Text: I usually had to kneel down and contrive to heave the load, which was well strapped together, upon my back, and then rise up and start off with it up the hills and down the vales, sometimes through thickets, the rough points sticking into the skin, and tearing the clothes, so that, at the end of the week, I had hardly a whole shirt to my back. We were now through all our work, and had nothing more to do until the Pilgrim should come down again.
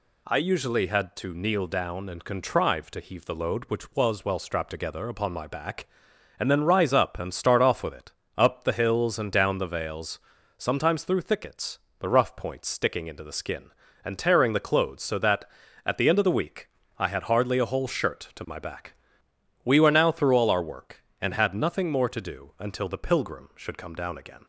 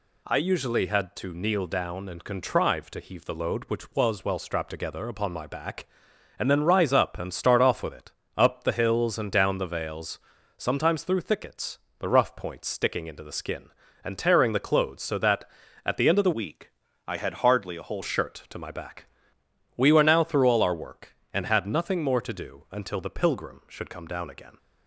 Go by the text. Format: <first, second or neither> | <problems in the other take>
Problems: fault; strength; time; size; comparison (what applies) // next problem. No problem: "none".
first | pauses between "it" and "up"; slight; at 8.1 s; 0.26 s long; slight in the first // changes voice from "week" to "whole"; from 16.3 to 18.0 s; 1.7 s long